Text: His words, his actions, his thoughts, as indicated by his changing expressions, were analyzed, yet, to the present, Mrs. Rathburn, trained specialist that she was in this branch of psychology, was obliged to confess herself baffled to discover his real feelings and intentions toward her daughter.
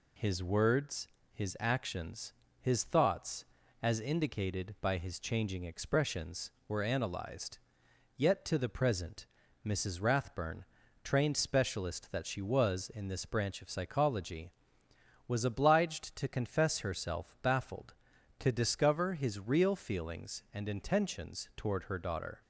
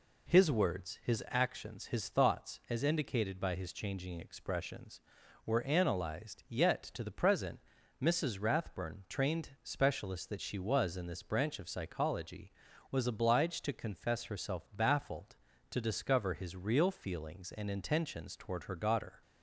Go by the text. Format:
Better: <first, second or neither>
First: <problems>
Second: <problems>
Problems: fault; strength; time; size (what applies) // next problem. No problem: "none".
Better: neither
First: none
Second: none